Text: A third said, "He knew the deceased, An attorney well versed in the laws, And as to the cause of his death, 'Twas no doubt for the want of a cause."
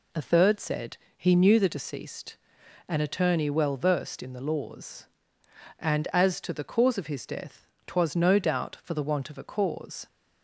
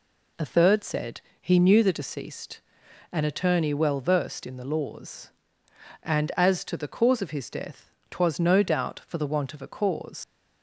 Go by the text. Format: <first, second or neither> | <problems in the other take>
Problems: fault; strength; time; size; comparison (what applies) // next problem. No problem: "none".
first | leaves "cause" unfinished; at 10.2 s; 70 ms